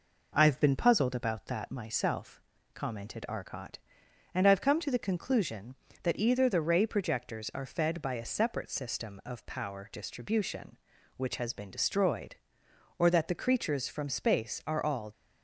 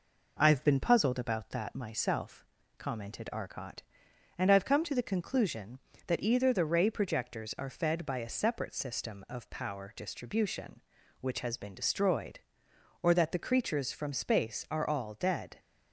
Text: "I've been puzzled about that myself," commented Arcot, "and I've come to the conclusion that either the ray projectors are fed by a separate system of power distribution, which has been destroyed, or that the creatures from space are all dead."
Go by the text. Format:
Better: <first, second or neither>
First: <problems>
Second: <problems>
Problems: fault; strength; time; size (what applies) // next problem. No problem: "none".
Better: second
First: stops before "dead"; at 15.1 s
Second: none